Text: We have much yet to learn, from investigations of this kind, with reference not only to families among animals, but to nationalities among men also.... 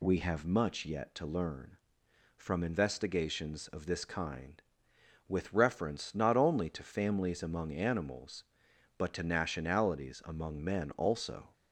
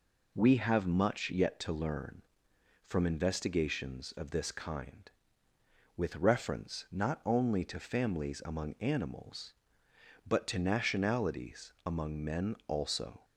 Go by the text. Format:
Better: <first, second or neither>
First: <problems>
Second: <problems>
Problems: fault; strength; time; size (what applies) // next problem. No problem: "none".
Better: neither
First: none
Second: none